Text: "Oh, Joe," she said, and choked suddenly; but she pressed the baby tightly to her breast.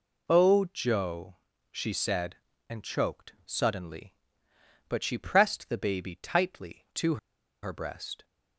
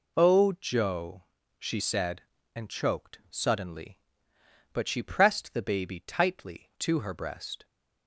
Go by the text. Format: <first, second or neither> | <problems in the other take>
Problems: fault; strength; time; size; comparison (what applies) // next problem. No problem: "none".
second | pauses between "to" and "her"; noticeable; at 7.1 s; 0.46 s long